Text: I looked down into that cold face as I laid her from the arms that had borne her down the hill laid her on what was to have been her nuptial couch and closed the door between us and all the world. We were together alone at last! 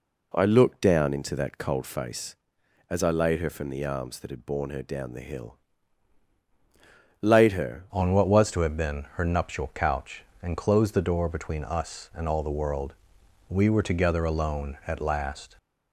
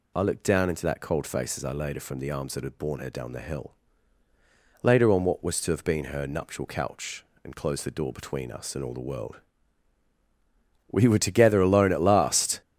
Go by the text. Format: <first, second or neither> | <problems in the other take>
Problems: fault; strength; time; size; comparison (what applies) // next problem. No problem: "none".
second | pauses between "hill" and "laid"; strong; at 5.5 s; 1.6 s long; also in the second // changes voice at "on"; from 7.9 s on; 7.6 s long